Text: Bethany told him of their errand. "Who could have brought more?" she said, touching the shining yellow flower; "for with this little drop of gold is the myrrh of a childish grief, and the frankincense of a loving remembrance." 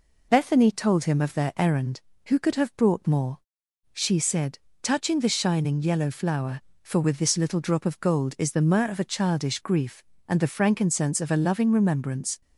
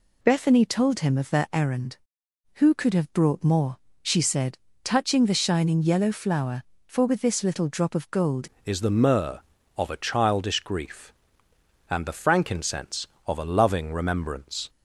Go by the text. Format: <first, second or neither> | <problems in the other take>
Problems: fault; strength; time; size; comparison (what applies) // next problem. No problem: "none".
first | changes voice at "is"; from 8.6 s on; 6.0 s long